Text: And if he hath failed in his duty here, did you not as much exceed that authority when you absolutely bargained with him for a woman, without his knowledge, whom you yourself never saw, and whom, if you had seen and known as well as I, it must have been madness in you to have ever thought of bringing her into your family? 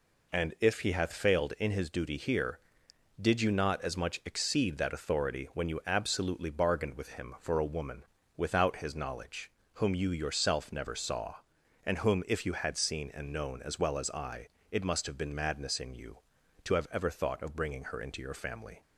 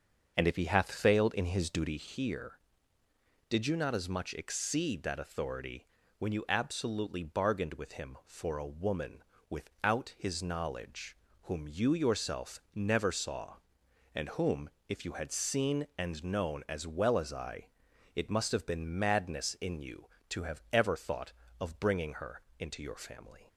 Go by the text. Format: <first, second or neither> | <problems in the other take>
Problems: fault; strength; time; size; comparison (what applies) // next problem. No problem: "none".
first | starts louder than the rest; until 2.2 s; 6.5 dB // pauses between "authority" and "when"; slight; at 5.8 s; 0.32 s long // pauses between "her" and "into"; slight; at 22.4 s; 0.18 s long